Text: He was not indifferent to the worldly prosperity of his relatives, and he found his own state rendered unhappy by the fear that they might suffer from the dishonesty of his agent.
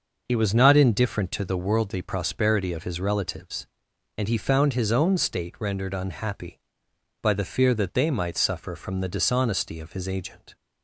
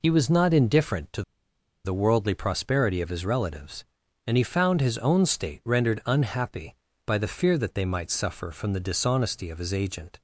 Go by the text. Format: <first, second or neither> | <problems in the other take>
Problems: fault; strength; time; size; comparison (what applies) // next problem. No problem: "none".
first | pauses between "to" and "the"; noticeable; at 1.2 s; 0.63 s long